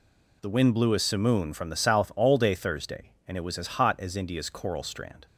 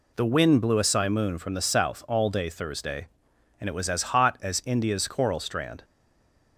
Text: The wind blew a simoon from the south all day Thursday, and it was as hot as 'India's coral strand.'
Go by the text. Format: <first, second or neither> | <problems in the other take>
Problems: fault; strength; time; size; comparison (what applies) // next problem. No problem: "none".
first | stays silent after the last word; slight; from 5.8 s on; 0.7 s long